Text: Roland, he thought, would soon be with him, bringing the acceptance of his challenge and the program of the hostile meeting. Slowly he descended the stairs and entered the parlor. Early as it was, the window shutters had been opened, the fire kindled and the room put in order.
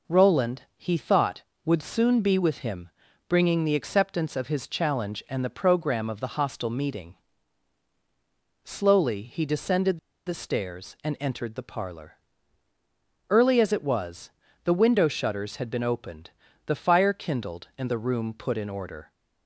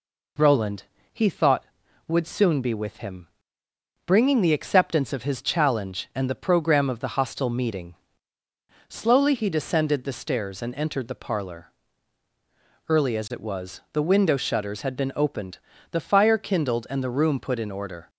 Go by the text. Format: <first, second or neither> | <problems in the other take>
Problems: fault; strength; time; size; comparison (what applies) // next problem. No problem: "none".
second | pauses between "descended" and "the"; slight; at 9.9 s; 0.29 s long